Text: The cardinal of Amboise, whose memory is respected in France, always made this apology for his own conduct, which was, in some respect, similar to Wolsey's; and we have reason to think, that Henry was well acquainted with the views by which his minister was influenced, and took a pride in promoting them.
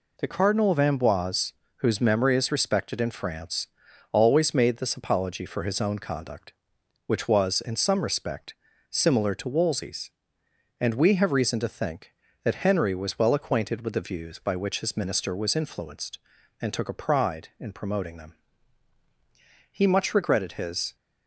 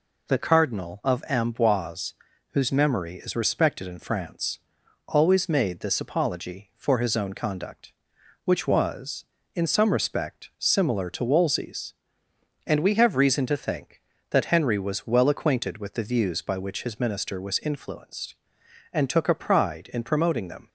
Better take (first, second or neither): second